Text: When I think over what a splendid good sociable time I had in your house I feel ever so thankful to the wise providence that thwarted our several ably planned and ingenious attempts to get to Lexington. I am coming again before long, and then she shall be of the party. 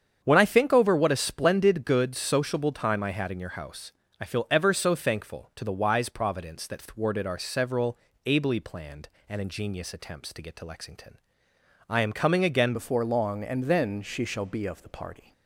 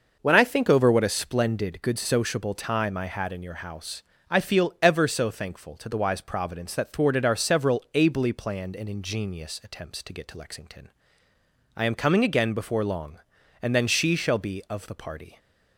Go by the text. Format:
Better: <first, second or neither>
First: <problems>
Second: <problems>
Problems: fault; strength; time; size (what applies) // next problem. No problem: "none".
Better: second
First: starts louder than the rest; strong; until 1.2 s; 8 dB // pauses between "house" and "I"; slight; at 3.9 s; 0.28 s long // pauses between "several" and "ably"; slight; at 7.9 s; 0.30 s long // changes voice at "before"; from 12.7 s on; 2.6 s long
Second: pauses between "house" and "I"; slight; at 4.0 s; 0.28 s long